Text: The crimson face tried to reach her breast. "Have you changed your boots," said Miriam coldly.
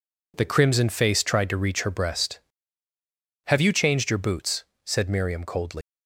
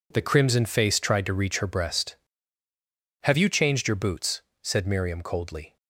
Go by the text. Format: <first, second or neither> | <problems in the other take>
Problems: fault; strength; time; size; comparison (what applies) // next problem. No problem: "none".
second | leaves "coldly" unfinished; at 5.8 s; 175 ms